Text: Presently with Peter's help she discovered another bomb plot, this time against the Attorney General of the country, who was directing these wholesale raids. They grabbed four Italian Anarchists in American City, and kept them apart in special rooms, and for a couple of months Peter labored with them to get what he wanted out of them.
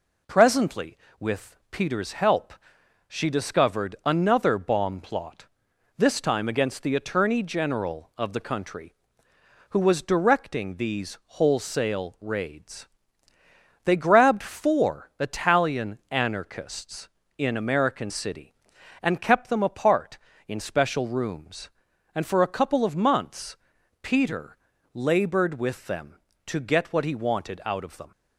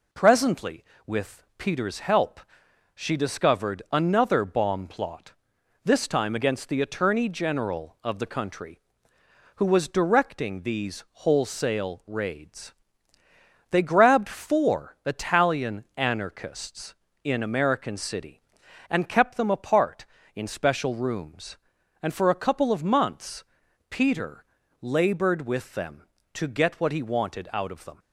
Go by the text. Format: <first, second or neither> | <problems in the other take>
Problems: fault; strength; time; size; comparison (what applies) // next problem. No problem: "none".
neither | pauses between "help" and "she"; noticeable; the same in both // pauses between "months" and "Peter"; noticeable; the same in both // pauses between "Peter" and "labored"; slight; the same in both